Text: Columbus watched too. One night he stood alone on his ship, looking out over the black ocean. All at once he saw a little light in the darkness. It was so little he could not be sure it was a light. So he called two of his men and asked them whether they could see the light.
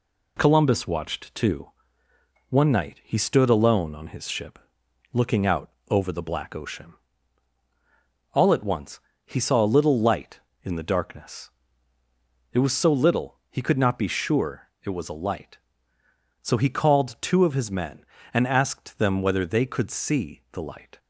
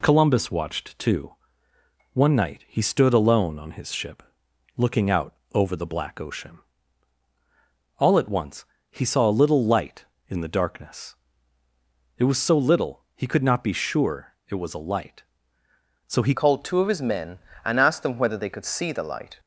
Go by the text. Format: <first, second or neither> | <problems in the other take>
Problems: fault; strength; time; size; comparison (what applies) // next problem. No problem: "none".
first | pauses between "out" and "over"; slight; at 5.3 s; 0.18 s long; slight in the first // pauses between "once" and "he"; slight; at 8.6 s; 0.24 s long; slight in the first // pauses between "sure" and "it"; slight; at 14.3 s; 0.16 s long; slight in the first // changes voice at "called"; from 16.3 s on; 3.0 s long